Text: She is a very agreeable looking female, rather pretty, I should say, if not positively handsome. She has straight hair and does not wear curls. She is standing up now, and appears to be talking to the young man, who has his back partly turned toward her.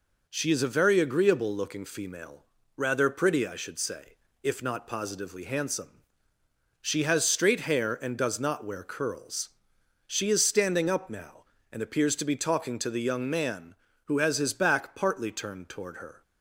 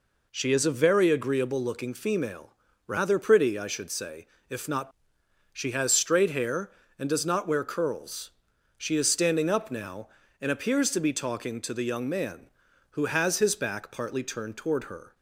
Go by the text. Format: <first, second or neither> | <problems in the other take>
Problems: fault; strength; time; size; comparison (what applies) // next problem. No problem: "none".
first | skips "positively handsome"; at 5.2 s